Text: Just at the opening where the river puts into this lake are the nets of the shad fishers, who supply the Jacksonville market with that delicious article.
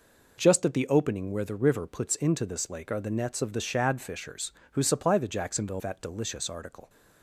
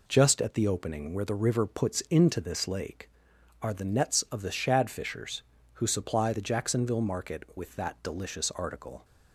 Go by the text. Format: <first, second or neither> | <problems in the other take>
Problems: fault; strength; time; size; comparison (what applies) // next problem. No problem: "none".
second | skips "market with"; at 5.8 s